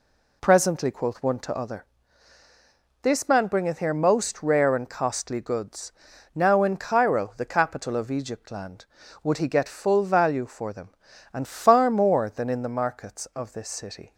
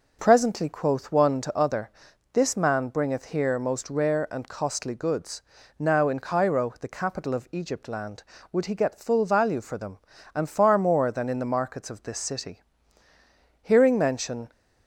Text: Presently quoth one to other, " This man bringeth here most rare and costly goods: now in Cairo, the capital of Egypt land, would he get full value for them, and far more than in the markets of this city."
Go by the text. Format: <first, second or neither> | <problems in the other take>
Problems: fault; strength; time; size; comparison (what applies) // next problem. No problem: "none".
first | goes on to say "Hearing mention"; noticeable; from 13.6 s on; 0.88 s long